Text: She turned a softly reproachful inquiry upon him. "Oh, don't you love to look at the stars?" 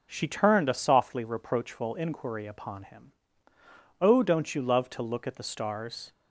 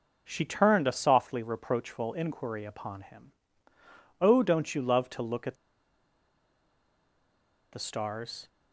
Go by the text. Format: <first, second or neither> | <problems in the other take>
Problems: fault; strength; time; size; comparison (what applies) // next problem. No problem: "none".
first | pauses between "at" and "the"; strong; at 5.5 s; 2.1 s long